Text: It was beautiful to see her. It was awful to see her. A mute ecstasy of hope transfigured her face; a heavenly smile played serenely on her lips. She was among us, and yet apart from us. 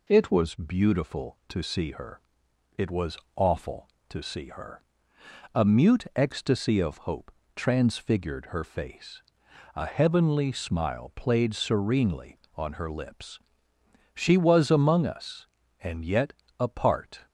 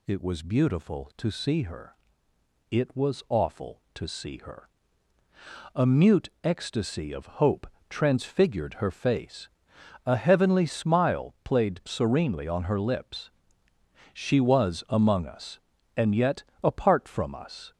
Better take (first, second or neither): second